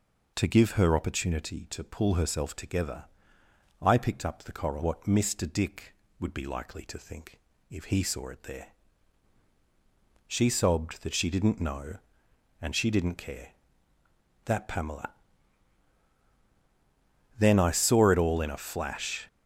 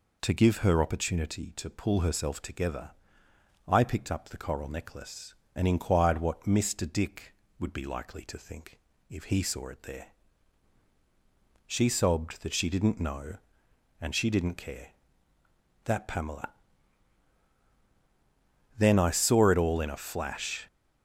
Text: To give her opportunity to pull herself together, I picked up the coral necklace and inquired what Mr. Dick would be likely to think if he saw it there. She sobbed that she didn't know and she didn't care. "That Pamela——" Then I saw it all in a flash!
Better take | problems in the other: second | skips "necklace and inquired"; at 4.8 s // pauses between "think" and "if"; slight; at 7.3 s; 0.30 s long; slight in the second

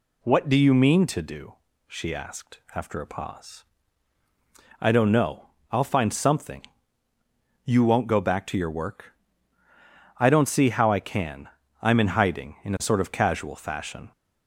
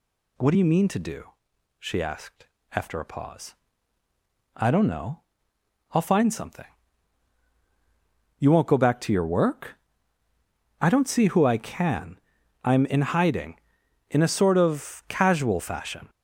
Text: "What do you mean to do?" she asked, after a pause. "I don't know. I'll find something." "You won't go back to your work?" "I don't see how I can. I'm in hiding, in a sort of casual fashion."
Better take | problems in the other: first | says "who" for "how"; at 11.2 s

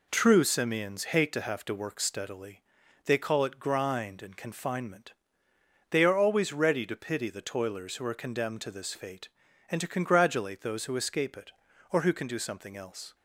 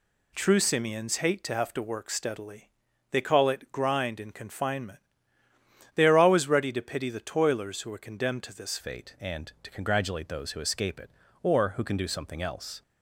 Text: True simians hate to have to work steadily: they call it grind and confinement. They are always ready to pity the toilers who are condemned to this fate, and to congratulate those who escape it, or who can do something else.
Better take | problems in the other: first | changes voice at "fate"; from 8.8 s on; 4.0 s long

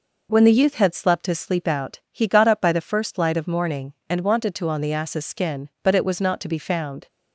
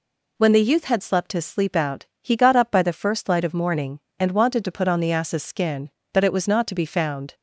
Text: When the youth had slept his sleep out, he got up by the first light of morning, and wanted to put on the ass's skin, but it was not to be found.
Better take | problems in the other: second | skips "put"; at 4.6 s

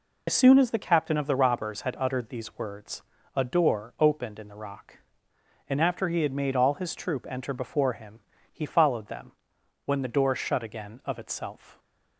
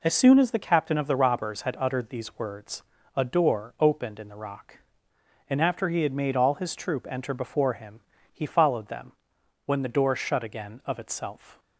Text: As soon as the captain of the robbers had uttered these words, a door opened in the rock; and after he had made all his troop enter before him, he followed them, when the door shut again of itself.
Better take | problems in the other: second | loses the start of "As"; at 0.2 s; 50 ms

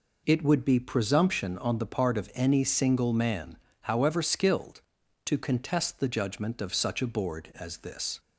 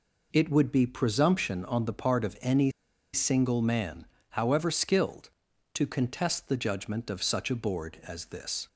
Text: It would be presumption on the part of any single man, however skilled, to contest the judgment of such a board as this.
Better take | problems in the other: first | pauses between "any" and "single"; at 2.7 s; 0.41 s long

